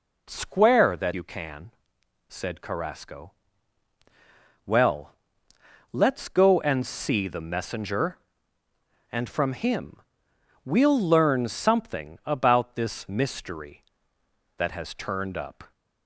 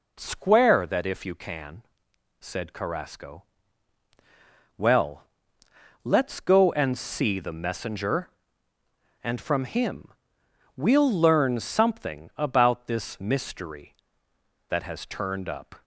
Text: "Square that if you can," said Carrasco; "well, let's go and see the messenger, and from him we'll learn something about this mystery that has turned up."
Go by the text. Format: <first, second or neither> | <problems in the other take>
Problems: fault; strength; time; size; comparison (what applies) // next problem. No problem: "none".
second | skips "if"; at 1.1 s // pauses between "him" and "we'll"; noticeable; at 10.0 s; 0.64 s long; noticeable in the second